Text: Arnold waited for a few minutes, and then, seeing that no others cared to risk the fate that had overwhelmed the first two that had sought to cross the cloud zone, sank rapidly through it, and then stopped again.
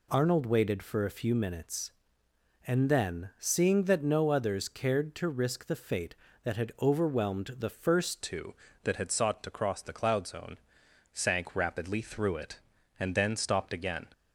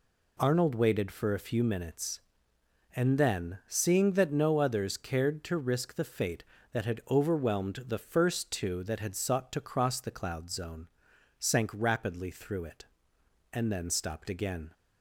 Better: second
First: changes voice at "two"; from 8.2 s on; 5.8 s long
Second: none

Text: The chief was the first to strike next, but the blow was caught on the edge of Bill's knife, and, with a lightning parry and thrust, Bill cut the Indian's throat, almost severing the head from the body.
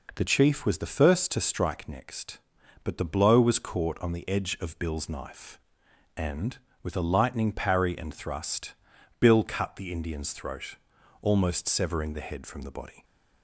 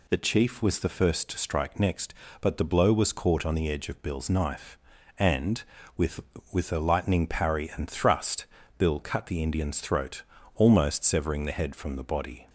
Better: first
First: none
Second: says "with" twice; at 6.5 s

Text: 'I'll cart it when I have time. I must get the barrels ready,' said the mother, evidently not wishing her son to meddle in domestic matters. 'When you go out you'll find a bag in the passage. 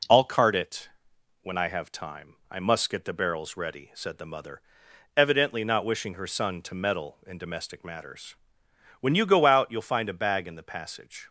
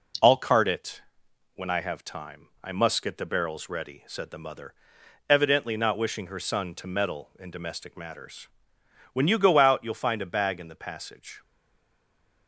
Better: first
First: pauses between "it" and "when"; noticeable; at 0.8 s; 0.54 s long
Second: pauses between "it" and "when"; noticeable; at 1.0 s; 0.54 s long // stays silent after the last word; from 11.4 s on; 1.0 s long

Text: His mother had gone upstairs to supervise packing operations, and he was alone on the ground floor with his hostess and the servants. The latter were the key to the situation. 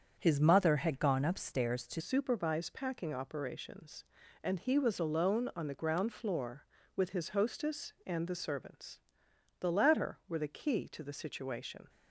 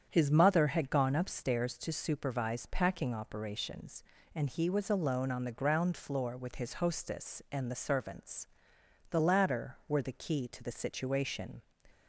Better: second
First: starts louder than the rest; strong; until 1.2 s; 7 dB // changes voice at "supervise"; from 1.9 s on; 9.9 s long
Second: starts louder than the rest; strong; until 1.1 s; 8.5 dB

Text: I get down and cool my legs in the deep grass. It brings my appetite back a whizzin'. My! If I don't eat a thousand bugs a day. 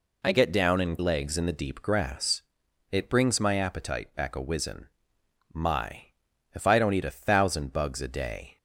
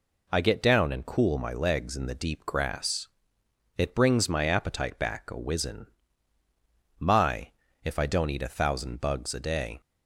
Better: second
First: skips "cool my"; at 0.9 s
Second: none

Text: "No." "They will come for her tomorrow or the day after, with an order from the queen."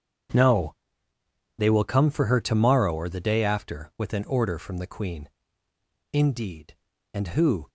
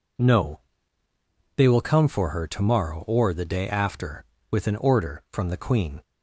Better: second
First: starts louder than the rest; strong; until 2.1 s; 8 dB // goes on to say "Indeed And who"; from 6.1 s on; 1.5 s long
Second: none

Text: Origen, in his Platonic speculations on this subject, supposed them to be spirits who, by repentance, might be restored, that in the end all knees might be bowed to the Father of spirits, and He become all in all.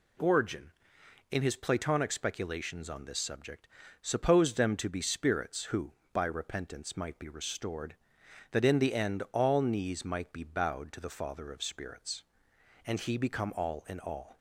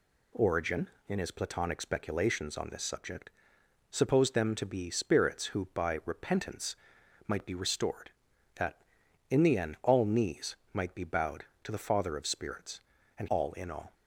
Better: first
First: none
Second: pauses between "knees" and "might"; slight; at 10.5 s; 0.18 s long // skips "He become"; at 13.2 s

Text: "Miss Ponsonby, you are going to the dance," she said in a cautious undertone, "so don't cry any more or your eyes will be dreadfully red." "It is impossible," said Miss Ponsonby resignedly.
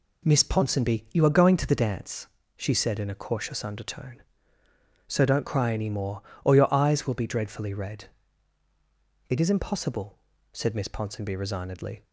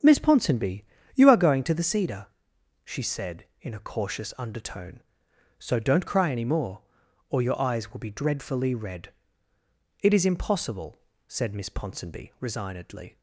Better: first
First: none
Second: starts louder than the rest; strong; until 1.3 s; 7.5 dB // says "cedar" for "dance"; at 1.8 s

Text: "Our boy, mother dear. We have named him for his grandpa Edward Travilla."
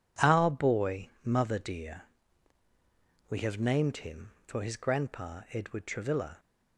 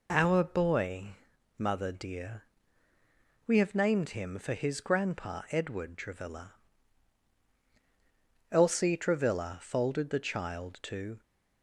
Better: first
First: none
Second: goes on to say "Elsie Travilla folded the child to"; strong; from 8.5 s on; 2.7 s long

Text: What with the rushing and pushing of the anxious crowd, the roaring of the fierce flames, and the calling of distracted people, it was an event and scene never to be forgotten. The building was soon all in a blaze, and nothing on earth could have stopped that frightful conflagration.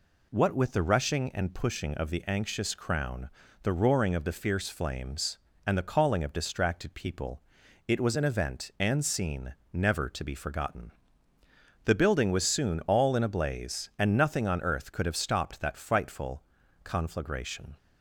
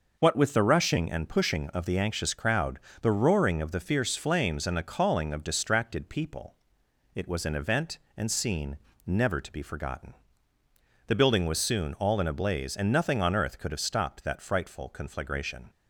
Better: second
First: says "crown" for "crowd"; at 2.7 s // pauses between "scene" and "never"; slight; at 9.5 s; 0.20 s long // pauses between "frightful" and "conflagration"; at 16.4 s; 0.40 s long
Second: pauses between "scene" and "never"; slight; at 8.7 s; 0.28 s long

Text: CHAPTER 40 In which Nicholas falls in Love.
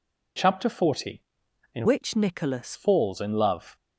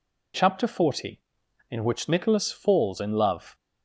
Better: second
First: changes voice from "which" to "Nicholas"; from 1.8 to 2.7 s; 0.9 s long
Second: none

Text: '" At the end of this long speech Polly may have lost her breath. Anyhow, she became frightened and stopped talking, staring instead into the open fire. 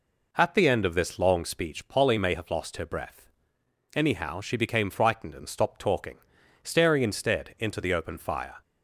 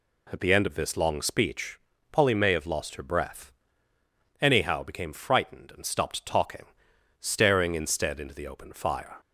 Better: first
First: none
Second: pauses between "speech" and "Polly"; slight; at 1.7 s; 0.32 s long // skips "she"; at 4.8 s

